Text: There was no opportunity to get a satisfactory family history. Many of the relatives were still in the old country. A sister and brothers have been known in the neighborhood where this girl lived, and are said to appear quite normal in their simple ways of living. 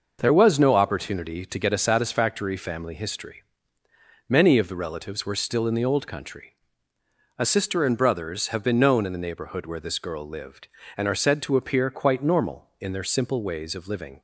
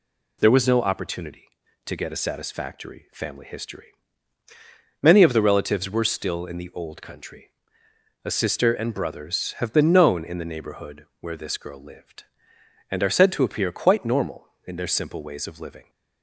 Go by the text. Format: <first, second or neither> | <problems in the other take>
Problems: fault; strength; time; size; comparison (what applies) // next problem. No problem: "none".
neither | none